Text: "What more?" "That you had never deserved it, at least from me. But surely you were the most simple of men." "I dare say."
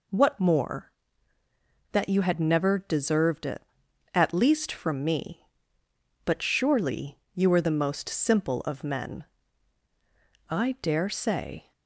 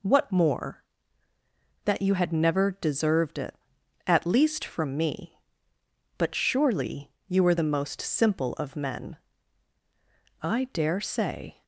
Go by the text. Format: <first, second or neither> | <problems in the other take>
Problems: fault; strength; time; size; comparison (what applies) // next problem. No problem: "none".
neither | pauses between "surely" and "you"; slight; the same in both